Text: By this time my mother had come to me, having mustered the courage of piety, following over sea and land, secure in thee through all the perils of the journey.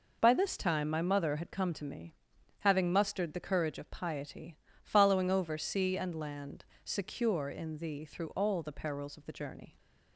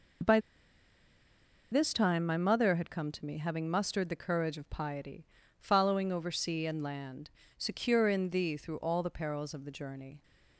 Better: first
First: none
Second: pauses between "By" and "this"; strong; at 0.3 s; 1.3 s long

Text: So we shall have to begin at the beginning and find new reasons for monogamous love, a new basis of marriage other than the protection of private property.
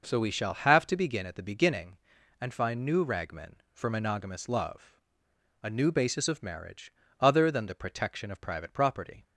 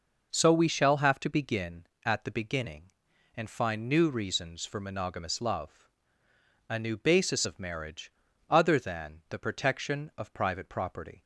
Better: second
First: says "ragmen" for "reasons"; at 3.0 s // pauses between "marriage" and "other"; slight; at 6.9 s; 0.30 s long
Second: pauses between "marriage" and "other"; at 8.1 s; 0.38 s long

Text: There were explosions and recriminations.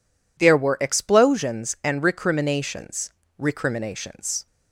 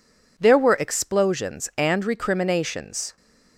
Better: second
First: says "recriminations" twice; at 3.3 s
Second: none

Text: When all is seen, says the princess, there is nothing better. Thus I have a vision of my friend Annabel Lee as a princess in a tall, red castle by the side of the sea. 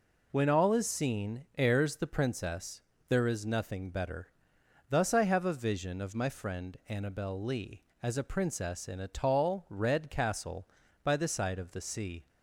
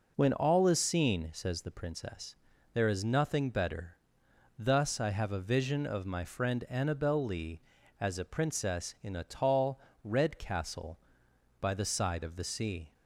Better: second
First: says "heirs" for "says"; at 1.5 s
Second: none

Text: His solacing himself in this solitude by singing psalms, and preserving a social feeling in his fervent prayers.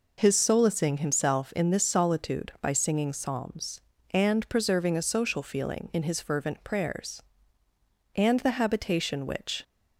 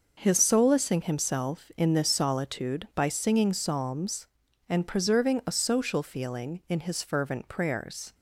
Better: second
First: goes on to say "And the habitation which"; from 8.1 s on; 1.4 s long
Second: none

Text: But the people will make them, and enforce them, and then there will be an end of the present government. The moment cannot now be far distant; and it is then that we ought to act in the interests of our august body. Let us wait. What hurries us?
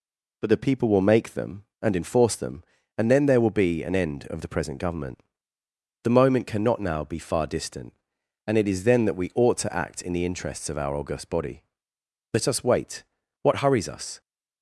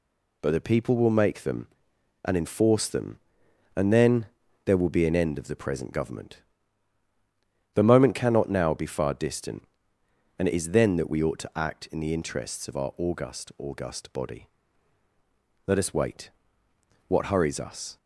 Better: first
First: none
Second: pauses between "then" and "there"; at 4.2 s; 0.38 s long // says "august" twice; at 13.5 s

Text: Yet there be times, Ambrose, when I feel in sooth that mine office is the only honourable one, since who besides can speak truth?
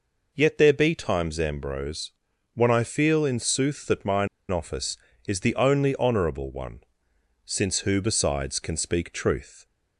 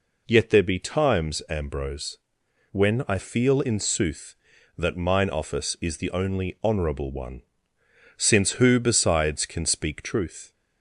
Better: second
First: pauses between "mine" and "office"; slight; at 4.2 s; 0.23 s long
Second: none

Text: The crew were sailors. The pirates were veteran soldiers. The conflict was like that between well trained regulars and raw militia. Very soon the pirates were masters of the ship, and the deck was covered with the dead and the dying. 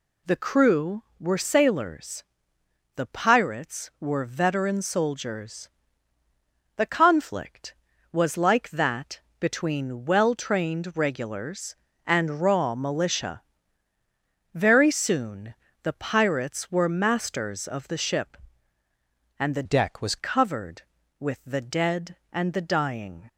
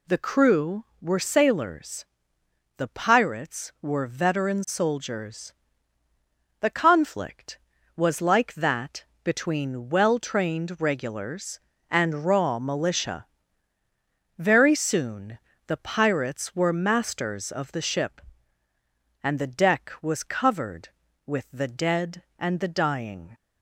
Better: second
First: pauses between "that" and "between"; slight; at 9.1 s; 0.20 s long // pauses between "soon" and "the"; slight; at 15.5 s; 0.26 s long // changes voice from "deck" to "was"; from 19.6 to 20.1 s; 0.5 s long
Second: pauses between "that" and "between"; slight; at 9.0 s; 0.20 s long // pauses between "soon" and "the"; slight; at 15.3 s; 0.26 s long

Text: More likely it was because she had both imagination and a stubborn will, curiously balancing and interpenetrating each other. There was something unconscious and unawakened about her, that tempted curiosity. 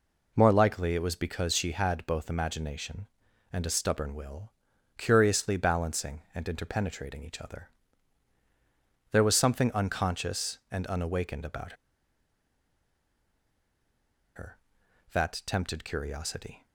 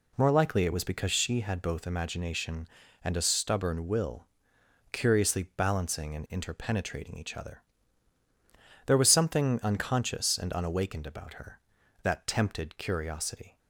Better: second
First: pauses between "about" and "her"; strong; at 11.7 s; 2.6 s long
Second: none

